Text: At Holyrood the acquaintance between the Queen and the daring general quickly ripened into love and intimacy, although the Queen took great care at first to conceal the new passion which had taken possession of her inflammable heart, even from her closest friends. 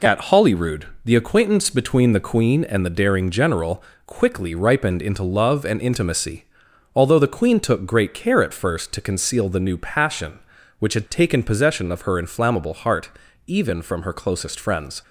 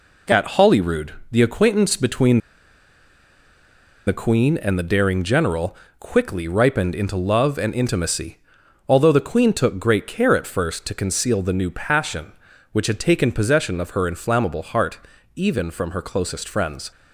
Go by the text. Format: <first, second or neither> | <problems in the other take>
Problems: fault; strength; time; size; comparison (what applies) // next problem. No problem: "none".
first | pauses between "Holyrood" and "the"; slight; at 1.1 s; 0.16 s long; slight in the first // pauses between "between" and "the"; strong; at 2.3 s; 1.6 s long // pauses between "general" and "quickly"; slight; at 5.7 s; 0.24 s long; slight in the first